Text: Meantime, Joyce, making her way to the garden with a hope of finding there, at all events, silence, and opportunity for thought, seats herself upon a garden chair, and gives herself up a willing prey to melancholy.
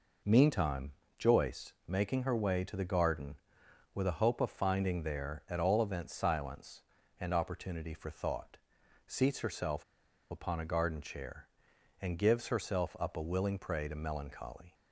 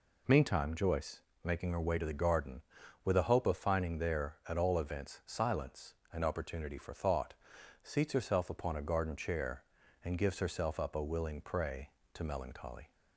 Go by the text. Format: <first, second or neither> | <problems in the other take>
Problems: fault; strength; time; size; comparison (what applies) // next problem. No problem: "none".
second | pauses between "herself" and "upon"; noticeable; at 9.8 s; 0.47 s long